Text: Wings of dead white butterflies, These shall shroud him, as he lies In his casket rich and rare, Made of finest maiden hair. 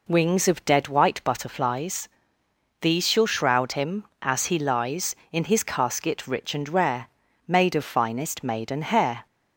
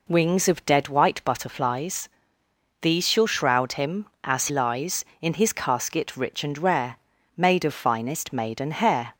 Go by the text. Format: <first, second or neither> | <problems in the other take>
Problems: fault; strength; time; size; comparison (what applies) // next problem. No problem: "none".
first | skips "he"; at 4.4 s